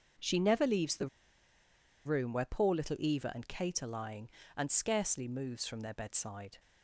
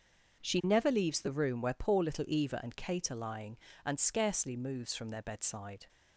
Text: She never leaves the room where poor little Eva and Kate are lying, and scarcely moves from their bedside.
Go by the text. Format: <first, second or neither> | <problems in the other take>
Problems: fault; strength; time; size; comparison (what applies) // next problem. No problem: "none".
second | starts louder than the rest; until 2.1 s; 6.5 dB; also in the second // pauses between "the" and "room"; noticeable; at 1.0 s; 0.97 s long